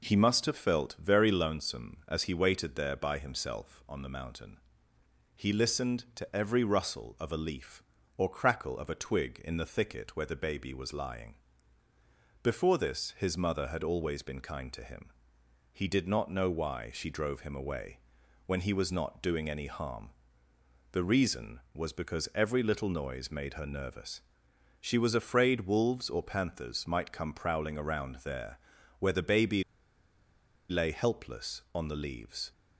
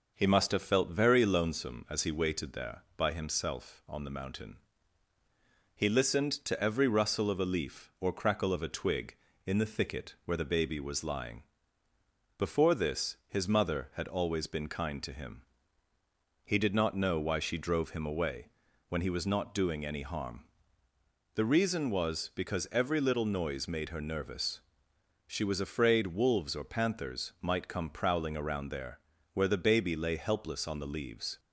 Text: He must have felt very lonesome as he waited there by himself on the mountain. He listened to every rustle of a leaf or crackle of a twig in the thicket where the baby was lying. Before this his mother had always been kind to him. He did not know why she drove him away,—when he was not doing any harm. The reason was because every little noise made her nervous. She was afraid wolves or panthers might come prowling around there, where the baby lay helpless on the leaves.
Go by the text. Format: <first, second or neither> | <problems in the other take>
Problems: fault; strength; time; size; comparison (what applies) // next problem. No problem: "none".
second | pauses between "baby" and "lay"; at 29.6 s; 1.0 s long